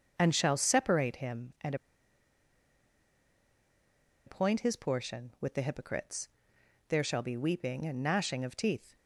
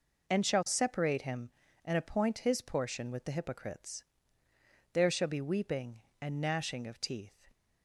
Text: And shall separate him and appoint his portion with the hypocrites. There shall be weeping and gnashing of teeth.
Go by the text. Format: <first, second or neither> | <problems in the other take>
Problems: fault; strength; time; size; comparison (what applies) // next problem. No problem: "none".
second | starts louder than the rest; until 1.1 s; 6.5 dB // pauses between "and" and "appoint"; strong; at 1.7 s; 2.5 s long